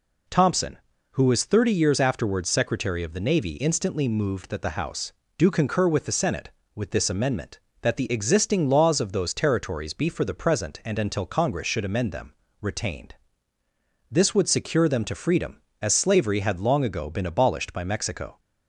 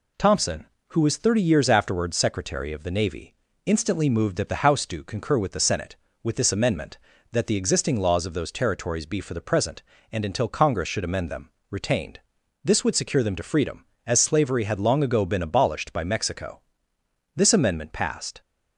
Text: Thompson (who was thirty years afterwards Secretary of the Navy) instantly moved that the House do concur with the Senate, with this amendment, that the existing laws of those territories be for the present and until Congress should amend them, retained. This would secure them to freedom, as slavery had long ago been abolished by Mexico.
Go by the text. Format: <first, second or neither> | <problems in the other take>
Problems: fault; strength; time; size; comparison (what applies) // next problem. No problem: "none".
first | goes on to say "This amendment passed"; noticeable; from 17.3 s on; 1.0 s long